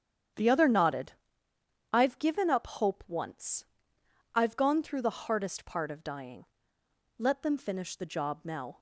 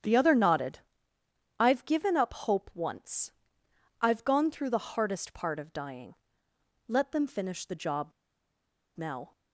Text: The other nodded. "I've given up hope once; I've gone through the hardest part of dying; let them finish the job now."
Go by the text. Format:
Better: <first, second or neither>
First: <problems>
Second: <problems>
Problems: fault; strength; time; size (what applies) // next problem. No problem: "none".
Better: first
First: starts louder than the rest; strong; until 2.1 s; 9 dB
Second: starts louder than the rest; strong; until 1.8 s; 9 dB // pauses between "job" and "now"; noticeable; at 8.1 s; 0.85 s long